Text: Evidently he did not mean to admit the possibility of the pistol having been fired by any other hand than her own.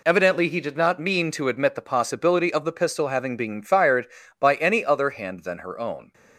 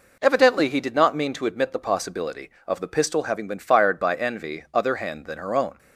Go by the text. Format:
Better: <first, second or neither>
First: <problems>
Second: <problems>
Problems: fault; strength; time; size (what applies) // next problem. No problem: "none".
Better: first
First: none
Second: says "envy" for "any"; at 4.1 s